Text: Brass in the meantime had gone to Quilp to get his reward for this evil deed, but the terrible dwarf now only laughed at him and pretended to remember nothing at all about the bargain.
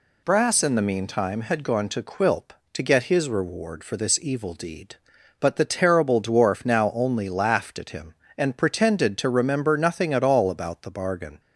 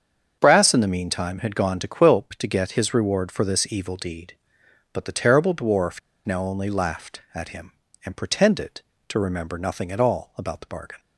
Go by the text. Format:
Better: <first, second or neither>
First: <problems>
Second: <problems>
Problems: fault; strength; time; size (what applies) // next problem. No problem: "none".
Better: first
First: none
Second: starts louder than the rest; until 1.4 s; 7 dB // pauses between "dwarf" and "now"; slight; at 5.9 s; 0.25 s long